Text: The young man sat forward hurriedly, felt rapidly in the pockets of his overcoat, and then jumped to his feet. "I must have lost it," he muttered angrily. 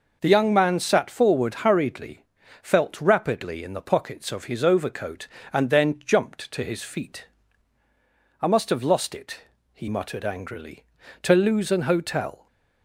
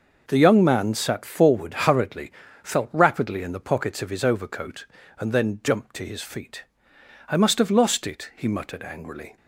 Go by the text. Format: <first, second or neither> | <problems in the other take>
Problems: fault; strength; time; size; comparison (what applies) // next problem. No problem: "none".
second | goes on to say "To lose an hotel"; noticeable; from 11.2 s on; 1.2 s long